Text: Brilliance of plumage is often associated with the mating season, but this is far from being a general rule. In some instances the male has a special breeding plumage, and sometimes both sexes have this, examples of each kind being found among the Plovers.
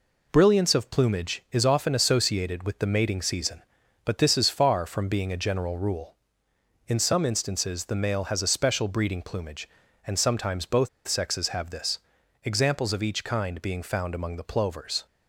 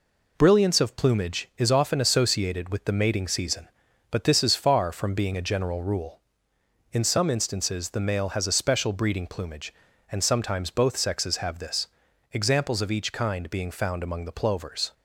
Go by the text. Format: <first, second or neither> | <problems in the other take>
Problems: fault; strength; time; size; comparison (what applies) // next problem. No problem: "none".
second | pauses between "both" and "sexes"; slight; at 10.8 s; 0.18 s long